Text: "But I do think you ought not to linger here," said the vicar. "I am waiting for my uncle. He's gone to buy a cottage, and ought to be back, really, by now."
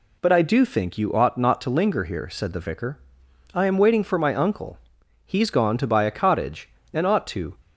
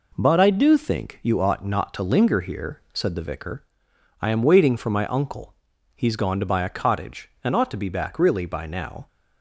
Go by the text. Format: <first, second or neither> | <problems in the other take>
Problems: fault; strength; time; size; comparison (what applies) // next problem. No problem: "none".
second | stops before "be back really by now"; at 7.6 s